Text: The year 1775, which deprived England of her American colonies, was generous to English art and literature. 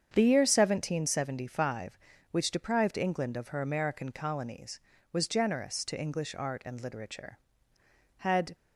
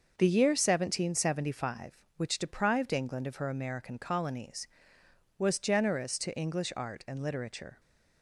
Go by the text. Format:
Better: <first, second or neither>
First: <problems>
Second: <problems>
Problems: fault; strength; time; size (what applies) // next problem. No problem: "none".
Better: second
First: starts louder than the rest; strong; until 1.1 s; 7.5 dB // goes on to say "Had"; slight; from 8.1 s on; 0.36 s long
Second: starts louder than the rest; noticeable; until 1.1 s; 6 dB